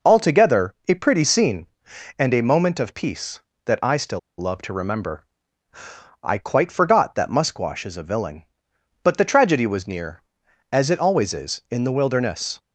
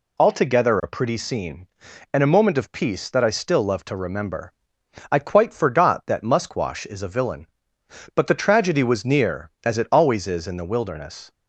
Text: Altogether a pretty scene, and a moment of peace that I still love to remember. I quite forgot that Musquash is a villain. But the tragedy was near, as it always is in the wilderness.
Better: second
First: pauses between "Altogether" and "a"; slight; at 0.7 s; 0.16 s long // pauses between "still" and "love"; slight; at 4.1 s; 0.20 s long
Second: none

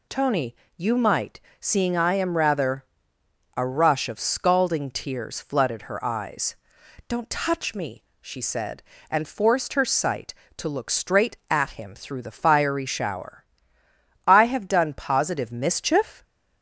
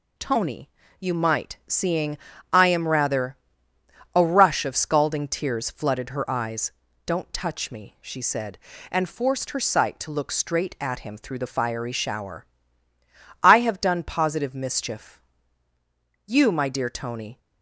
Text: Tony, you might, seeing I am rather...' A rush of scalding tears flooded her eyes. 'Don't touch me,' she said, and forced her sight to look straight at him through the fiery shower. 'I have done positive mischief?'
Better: first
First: none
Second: pauses between "seeing" and "I"; slight; at 2.1 s; 0.36 s long // goes on to say "You my dear Tony"; noticeable; from 16.2 s on; 1.1 s long

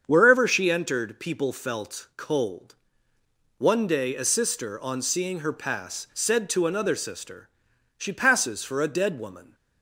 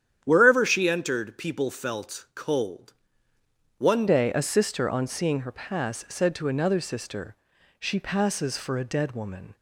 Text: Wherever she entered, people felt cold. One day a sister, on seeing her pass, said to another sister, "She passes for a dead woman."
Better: first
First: starts louder than the rest; strong; until 1.0 s; 7.5 dB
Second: starts louder than the rest; strong; until 1.2 s; 10 dB // changes voice at "day"; from 4.0 s on; 5.5 s long

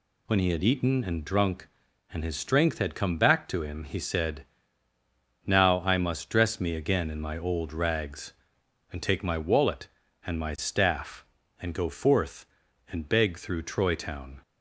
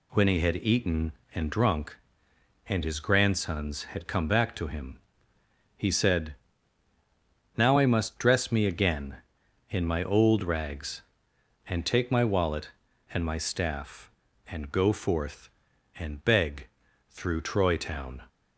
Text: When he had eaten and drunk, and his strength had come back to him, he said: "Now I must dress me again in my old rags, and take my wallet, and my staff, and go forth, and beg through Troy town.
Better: first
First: none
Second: says "grandsons" for "strength"; at 2.9 s // pauses between "beg" and "through"; at 16.6 s; 0.42 s long

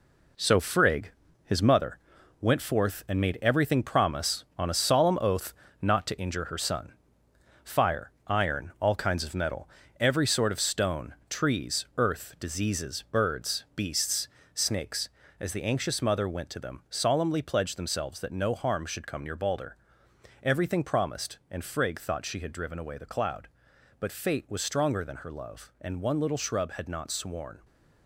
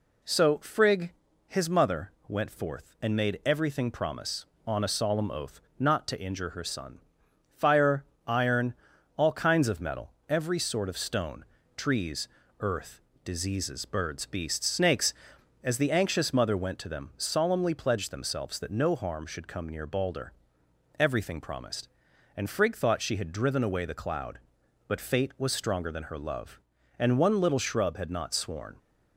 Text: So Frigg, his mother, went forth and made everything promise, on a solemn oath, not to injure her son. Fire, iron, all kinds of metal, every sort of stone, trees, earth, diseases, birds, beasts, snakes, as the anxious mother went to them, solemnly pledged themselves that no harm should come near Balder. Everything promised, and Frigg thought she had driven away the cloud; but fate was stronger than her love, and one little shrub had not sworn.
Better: second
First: gets quieter; strong; throughout; 7 dB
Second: none

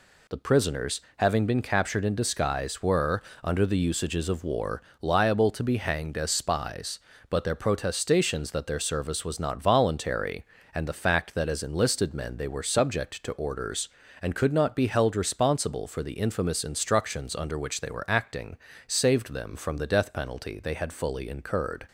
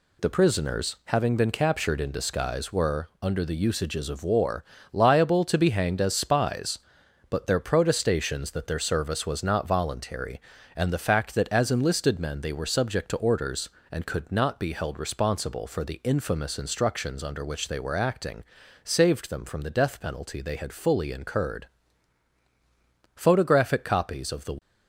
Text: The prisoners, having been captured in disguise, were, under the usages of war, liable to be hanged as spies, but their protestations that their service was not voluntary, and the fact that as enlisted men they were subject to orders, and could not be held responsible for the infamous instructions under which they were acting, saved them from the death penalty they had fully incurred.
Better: first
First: none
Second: goes on to say "Photographic copies of the"; from 23.1 s on; 1.4 s long

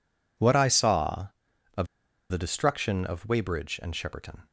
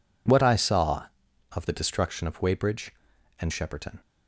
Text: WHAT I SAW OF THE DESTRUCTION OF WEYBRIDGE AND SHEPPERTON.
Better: second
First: pauses between "OF" and "THE"; at 1.8 s; 0.44 s long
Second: none

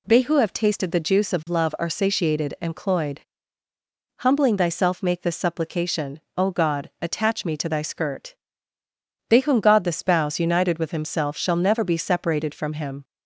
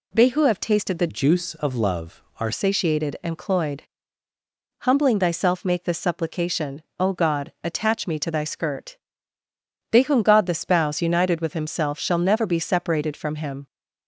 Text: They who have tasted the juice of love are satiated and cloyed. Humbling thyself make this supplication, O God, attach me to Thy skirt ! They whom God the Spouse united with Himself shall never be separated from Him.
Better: first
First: none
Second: changes voice from "juice" to "are"; from 1.0 to 2.5 s; 1.5 s long

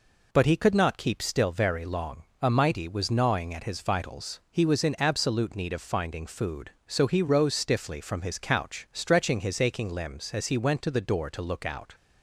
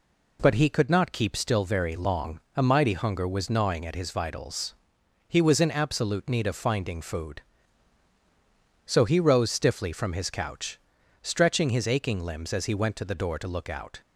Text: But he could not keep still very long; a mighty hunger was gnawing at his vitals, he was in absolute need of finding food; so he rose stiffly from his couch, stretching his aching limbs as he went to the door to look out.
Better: second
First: skips "hunger"; at 2.8 s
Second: none

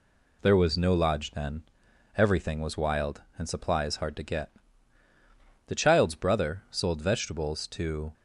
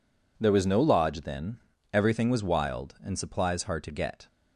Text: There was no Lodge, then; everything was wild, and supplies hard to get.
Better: second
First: goes on to say "The child's brother sold vegetables to"; strong; from 5.6 s on; 2.4 s long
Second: none

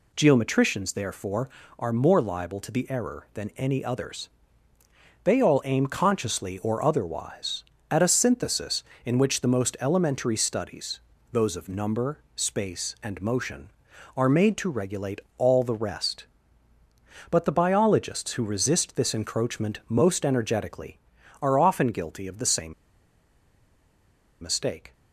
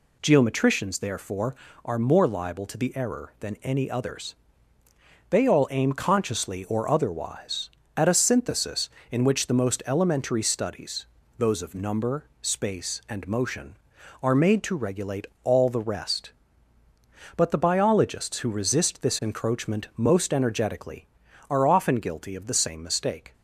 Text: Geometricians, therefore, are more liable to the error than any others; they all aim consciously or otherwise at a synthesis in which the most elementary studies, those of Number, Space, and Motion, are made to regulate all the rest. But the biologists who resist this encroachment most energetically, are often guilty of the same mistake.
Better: second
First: pauses between "regulate" and "all"; slight; at 15.2 s; 0.16 s long // pauses between "same" and "mistake"; strong; at 22.7 s; 1.6 s long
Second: pauses between "regulate" and "all"; slight; at 15.2 s; 0.16 s long

